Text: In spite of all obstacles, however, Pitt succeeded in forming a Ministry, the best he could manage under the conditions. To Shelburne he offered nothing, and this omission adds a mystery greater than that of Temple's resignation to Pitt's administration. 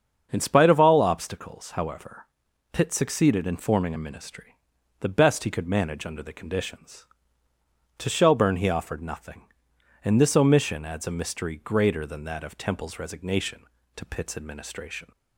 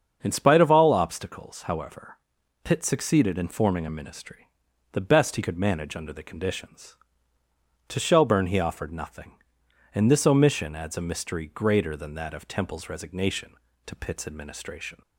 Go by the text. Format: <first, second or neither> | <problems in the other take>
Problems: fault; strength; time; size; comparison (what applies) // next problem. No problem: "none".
neither | starts louder than the rest; strong; the same in both